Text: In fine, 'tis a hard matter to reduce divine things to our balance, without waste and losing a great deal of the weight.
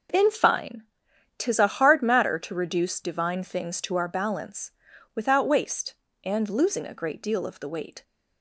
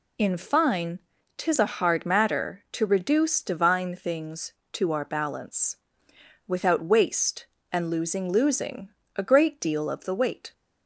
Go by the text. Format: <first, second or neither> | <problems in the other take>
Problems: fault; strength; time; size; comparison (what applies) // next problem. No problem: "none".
first | says "losing" twice; at 8.3 s